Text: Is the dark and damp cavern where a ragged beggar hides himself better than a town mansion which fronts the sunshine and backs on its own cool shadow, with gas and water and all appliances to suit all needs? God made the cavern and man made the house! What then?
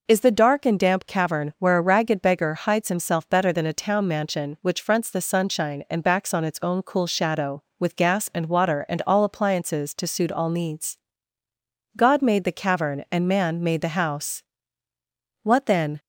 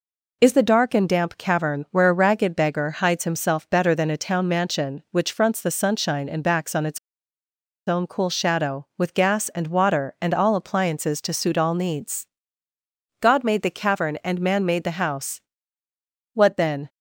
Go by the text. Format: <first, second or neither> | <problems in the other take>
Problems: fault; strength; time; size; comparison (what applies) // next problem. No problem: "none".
first | pauses between "its" and "own"; noticeable; at 6.9 s; 0.88 s long